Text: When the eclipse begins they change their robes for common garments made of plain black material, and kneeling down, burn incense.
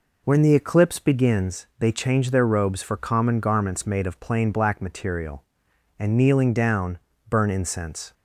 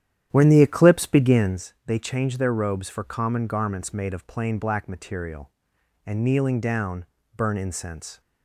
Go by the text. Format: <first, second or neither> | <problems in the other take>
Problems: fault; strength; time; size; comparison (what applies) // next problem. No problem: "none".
first | starts louder than the rest; strong; until 1.7 s; 10.5 dB